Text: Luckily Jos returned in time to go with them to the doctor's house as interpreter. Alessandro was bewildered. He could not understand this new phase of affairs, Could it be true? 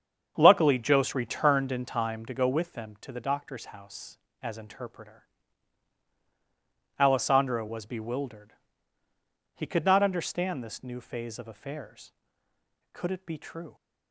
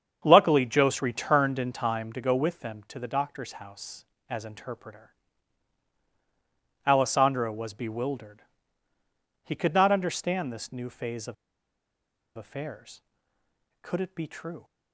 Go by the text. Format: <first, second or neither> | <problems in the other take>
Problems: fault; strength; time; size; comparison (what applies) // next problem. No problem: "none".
first | starts louder than the rest; strong; until 1.2 s; 7.5 dB; strong in the first // pauses between "of" and "affairs"; at 11.3 s; 1.0 s long